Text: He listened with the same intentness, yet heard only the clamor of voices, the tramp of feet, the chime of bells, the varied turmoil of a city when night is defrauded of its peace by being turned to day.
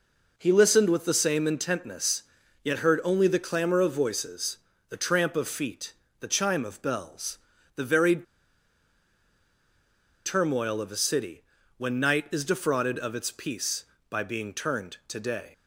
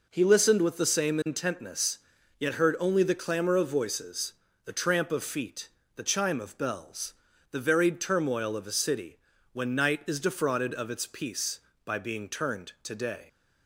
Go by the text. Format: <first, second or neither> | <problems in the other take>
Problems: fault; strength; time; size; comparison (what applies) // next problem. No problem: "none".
second | pauses between "varied" and "turmoil"; strong; at 8.2 s; 2.0 s long // pauses between "city" and "when"; slight; at 11.4 s; 0.36 s long; slight in the second